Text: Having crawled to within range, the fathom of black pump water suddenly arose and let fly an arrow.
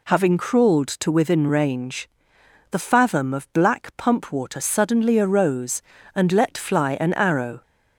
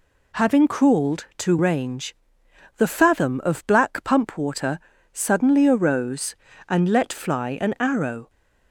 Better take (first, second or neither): first